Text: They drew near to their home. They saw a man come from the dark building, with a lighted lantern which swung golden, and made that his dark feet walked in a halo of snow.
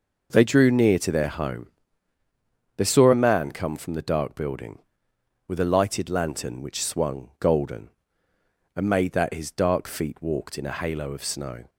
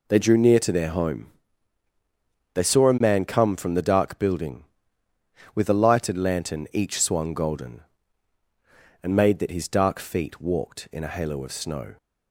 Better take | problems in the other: first | says "each" for "which"; at 6.7 s

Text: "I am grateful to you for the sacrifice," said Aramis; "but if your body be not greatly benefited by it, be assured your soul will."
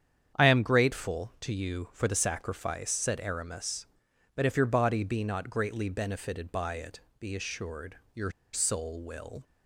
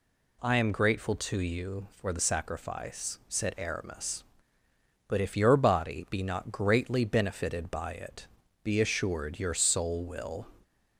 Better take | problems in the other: second | starts louder than the rest; strong; until 1.4 s; 8.5 dB // pauses between "assured" and "your"; slight; at 7.9 s; 0.16 s long // pauses between "your" and "soul"; slight; at 8.2 s; 0.23 s long

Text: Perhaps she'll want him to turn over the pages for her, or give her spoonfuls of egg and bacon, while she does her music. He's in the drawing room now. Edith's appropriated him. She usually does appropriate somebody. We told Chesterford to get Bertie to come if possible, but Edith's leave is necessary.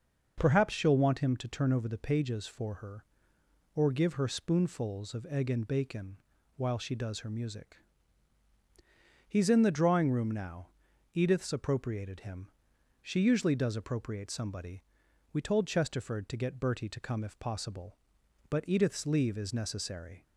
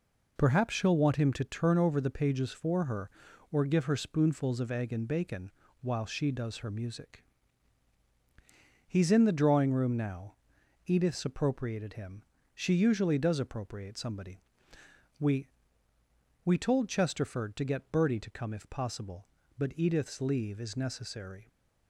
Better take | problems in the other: first | says "We" twice; at 16.4 s

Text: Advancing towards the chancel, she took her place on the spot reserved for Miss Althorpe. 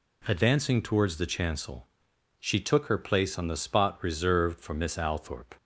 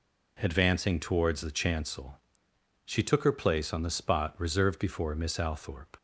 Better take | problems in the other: first | says "before" for "for"; at 4.7 s

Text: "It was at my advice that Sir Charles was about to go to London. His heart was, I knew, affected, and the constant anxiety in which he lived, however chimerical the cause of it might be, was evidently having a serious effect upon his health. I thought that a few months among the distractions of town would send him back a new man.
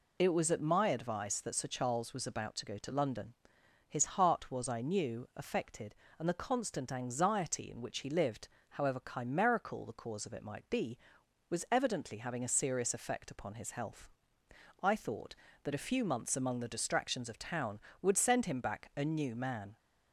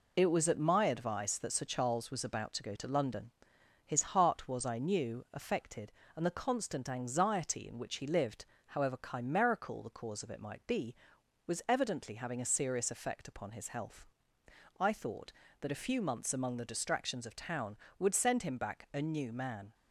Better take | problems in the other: first | gets quieter; noticeable; throughout; 5 dB

